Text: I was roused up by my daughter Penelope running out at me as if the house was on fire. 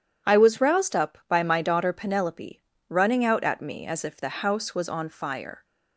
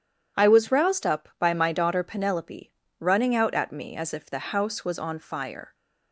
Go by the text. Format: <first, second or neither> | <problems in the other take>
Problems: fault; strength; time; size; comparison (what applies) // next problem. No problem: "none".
neither | starts louder than the rest; strong; the same in both // pauses between "Penelope" and "running"; slight; the same in both